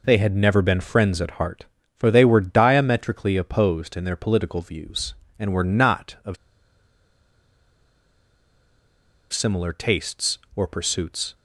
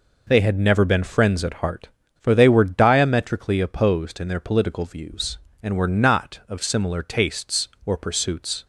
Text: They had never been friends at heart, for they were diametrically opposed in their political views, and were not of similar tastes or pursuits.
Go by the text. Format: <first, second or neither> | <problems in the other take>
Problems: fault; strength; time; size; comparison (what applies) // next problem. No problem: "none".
second | pauses between "of" and "similar"; strong; at 6.3 s; 2.9 s long